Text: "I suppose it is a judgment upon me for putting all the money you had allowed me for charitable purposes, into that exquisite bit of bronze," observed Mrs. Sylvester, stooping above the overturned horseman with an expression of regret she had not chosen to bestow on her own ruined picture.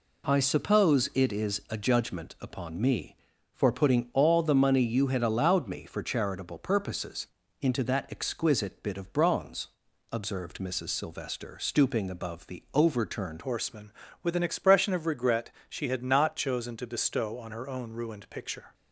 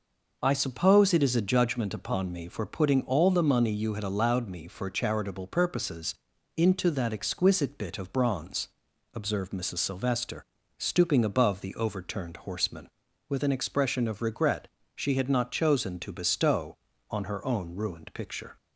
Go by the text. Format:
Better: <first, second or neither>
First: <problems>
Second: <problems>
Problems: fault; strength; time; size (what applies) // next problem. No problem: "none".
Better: second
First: changes voice at "horseman"; from 13.4 s on; 5.3 s long // pauses between "regret" and "she"; slight; at 15.4 s; 0.20 s long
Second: pauses between "regret" and "she"; slight; at 14.6 s; 0.30 s long